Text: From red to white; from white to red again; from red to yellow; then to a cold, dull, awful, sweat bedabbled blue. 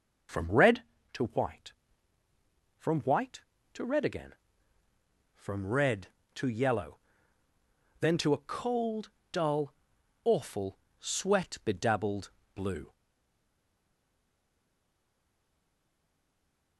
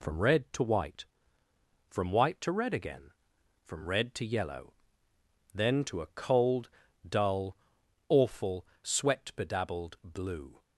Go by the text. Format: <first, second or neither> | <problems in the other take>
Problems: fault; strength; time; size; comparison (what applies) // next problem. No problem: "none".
second | pauses between "bedabbled" and "blue"; slight; at 12.2 s; 0.24 s long // stays silent after the last word; strong; from 12.9 s on; 3.8 s long